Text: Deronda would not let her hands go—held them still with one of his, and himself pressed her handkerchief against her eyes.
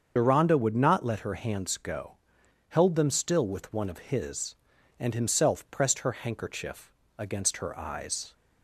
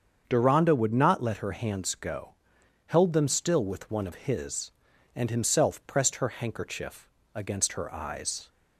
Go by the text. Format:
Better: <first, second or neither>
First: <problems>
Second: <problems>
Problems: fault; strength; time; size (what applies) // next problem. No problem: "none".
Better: second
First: loses the start of "Deronda"; at 0.1 s; 65 ms // starts louder than the rest; strong; until 1.1 s; 7 dB // pauses between "handkerchief" and "against"; slight; at 6.9 s; 0.26 s long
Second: starts louder than the rest; strong; until 1.2 s; 7.5 dB // pauses between "handkerchief" and "against"; slight; at 7.0 s; 0.26 s long